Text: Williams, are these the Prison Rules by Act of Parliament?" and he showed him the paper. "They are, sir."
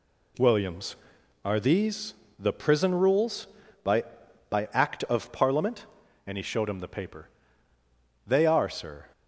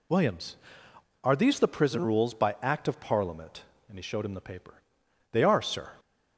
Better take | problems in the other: second | pauses between "these" and "the"; slight; at 2.1 s; 0.24 s long // says "by" twice; at 4.4 s

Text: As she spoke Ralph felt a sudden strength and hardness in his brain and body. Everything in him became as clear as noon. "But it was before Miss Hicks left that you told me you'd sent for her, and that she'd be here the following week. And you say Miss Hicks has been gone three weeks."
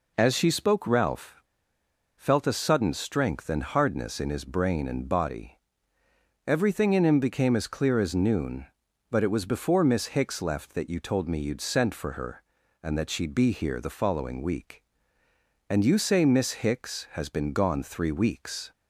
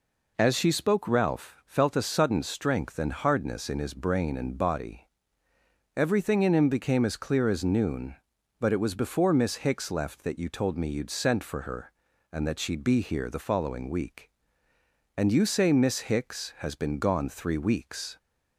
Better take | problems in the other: second | pauses between "Ralph" and "felt"; noticeable; at 1.4 s; 0.75 s long

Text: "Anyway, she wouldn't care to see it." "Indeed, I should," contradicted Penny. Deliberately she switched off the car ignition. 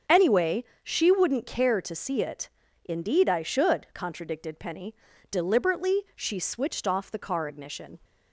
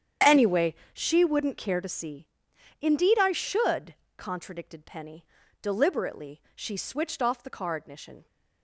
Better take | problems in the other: first | starts louder than the rest; strong; until 1.4 s; 8.5 dB; also in the first // skips "it"; at 2.5 s

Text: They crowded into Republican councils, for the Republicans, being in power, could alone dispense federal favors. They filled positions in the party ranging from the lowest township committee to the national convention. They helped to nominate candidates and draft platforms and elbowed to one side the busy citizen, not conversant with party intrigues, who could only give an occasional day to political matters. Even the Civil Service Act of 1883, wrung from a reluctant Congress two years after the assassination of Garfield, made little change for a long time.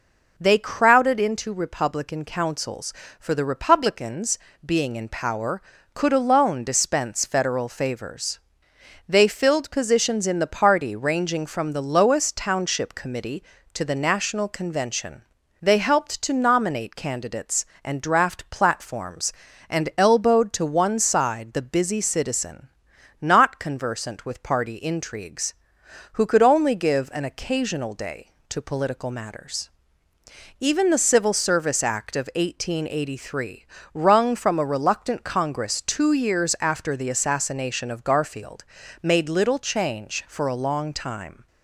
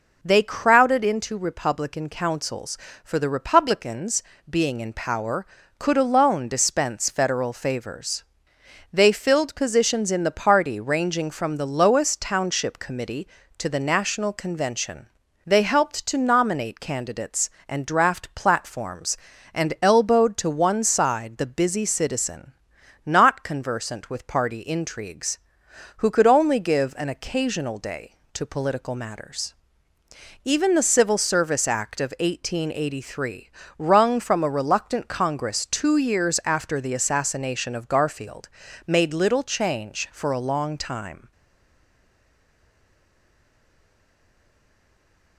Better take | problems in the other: first | stays silent after the last word; strong; from 41.3 s on; 4.0 s long

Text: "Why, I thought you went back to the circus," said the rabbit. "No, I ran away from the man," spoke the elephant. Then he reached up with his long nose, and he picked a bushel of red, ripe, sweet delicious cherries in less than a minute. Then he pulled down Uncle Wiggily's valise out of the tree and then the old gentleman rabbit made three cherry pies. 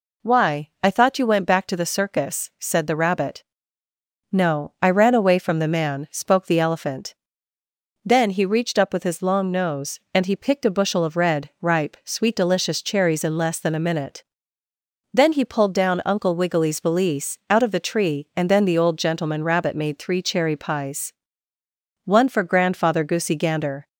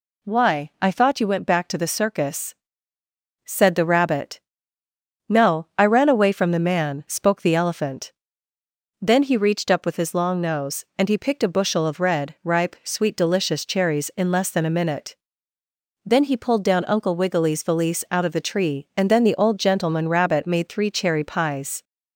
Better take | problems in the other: second | goes on to say "One for Grandfather Goosey Gander"; strong; from 22.0 s on; 1.8 s long

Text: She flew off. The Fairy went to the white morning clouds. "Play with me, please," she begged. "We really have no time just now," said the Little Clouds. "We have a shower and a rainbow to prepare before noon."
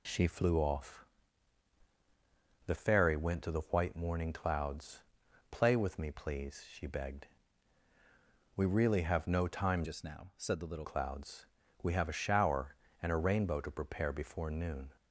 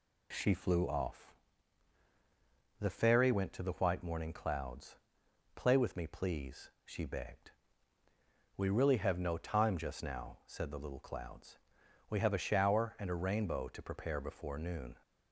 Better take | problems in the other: second | changes voice from "just" to "Little"; from 9.8 to 10.8 s; 1.0 s long

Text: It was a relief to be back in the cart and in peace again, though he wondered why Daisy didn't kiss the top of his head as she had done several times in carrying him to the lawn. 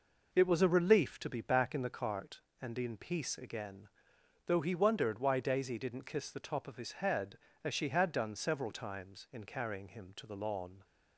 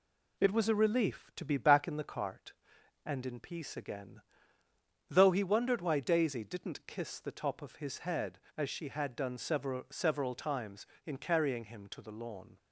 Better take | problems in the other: first | says "several" twice; at 9.8 s

